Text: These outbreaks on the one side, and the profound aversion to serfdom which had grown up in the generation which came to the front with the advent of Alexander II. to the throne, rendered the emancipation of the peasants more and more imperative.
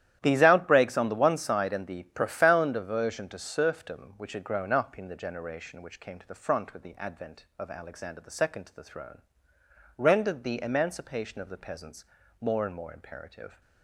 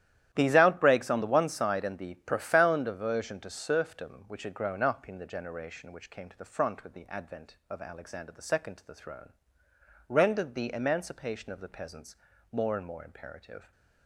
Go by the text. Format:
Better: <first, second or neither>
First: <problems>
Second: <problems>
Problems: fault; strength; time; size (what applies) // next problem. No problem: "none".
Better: neither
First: starts louder than the rest; strong; until 1.2 s; 11.5 dB // pauses between "peasants" and "more"; slight; at 12.0 s; 0.36 s long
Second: starts louder than the rest; strong; until 1.3 s; 12 dB // pauses between "peasants" and "more"; slight; at 12.1 s; 0.36 s long